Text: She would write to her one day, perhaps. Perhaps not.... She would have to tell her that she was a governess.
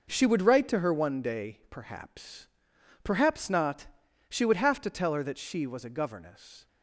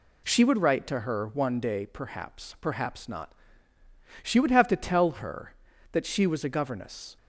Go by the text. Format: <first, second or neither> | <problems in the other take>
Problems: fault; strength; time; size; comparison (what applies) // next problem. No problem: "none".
neither | none